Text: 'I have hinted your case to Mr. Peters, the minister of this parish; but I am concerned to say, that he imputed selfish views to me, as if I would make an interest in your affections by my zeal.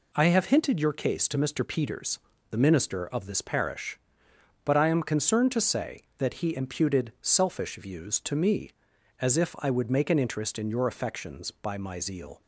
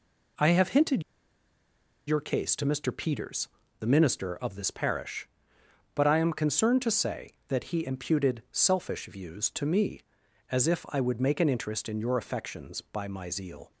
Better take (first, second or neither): first